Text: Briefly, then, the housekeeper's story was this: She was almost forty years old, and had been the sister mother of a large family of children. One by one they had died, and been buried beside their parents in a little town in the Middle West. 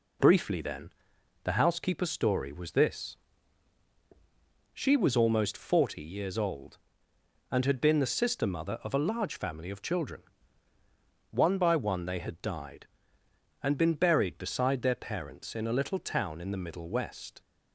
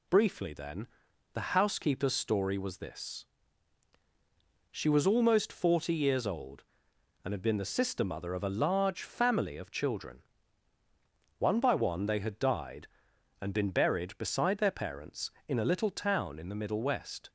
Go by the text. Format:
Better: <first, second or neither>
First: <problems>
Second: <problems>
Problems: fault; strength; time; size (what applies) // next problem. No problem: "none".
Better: neither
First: none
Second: none